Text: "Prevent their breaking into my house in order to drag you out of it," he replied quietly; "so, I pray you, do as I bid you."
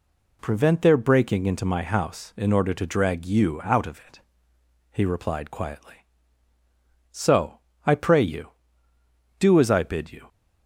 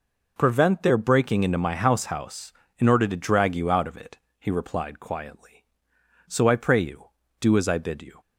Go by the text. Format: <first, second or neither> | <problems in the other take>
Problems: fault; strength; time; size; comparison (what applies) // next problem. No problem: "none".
first | says "house" twice; at 2.0 s